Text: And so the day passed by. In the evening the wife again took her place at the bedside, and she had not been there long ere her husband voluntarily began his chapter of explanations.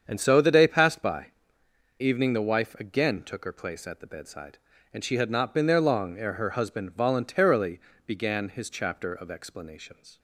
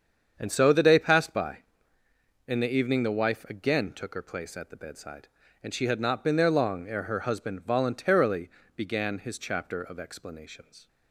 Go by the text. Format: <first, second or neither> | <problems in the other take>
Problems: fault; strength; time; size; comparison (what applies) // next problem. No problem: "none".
second | starts louder than the rest; strong; until 1.0 s; 7.5 dB; strong in the second // skips "In the"; at 1.6 s // pauses between "voluntarily" and "began"; slight; at 7.7 s; 0.28 s long; slight in the second